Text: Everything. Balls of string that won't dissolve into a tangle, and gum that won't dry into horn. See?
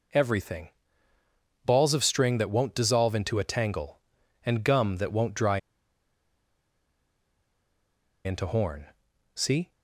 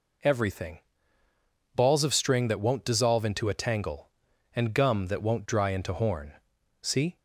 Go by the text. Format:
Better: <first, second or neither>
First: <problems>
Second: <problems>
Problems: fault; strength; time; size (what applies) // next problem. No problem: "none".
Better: second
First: pauses between "dry" and "into"; strong; at 5.5 s; 2.6 s long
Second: none